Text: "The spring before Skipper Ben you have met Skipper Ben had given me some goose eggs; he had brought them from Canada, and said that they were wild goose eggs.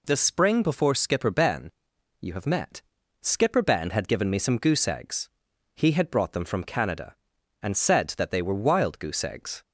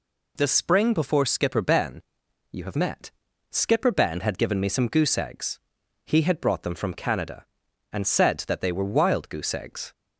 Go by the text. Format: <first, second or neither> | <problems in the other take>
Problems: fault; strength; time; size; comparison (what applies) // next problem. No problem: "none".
neither | pauses between "Ben" and "you"; noticeable; the same in both // pauses between "met" and "Skipper"; the same in both